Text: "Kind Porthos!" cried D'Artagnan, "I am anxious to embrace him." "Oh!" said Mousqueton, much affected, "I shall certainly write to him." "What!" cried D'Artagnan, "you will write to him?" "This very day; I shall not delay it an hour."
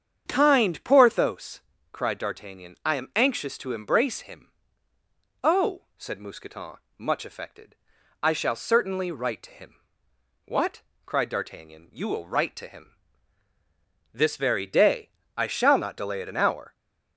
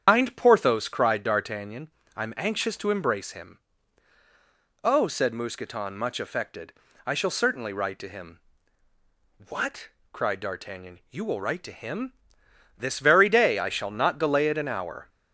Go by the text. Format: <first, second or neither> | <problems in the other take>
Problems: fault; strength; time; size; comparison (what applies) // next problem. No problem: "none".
first | loses the start of "Kind"; at 0.0 s; 115 ms // starts louder than the rest; strong; until 1.0 s; 8.5 dB; strong in the first